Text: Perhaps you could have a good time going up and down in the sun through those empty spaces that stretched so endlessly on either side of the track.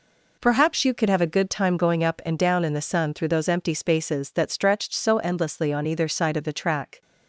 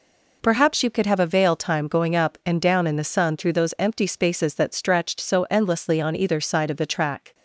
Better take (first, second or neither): first